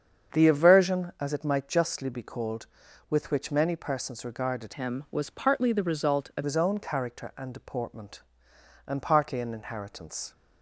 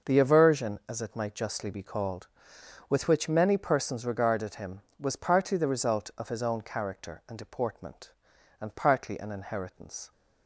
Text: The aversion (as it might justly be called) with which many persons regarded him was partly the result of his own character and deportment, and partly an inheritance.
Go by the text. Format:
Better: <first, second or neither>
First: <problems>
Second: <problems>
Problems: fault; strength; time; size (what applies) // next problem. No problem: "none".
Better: second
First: starts louder than the rest; strong; until 1.4 s; 7.5 dB // changes voice from "him" to "of"; from 4.7 to 6.4 s; 1.7 s long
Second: starts louder than the rest; noticeable; until 1.1 s; 6 dB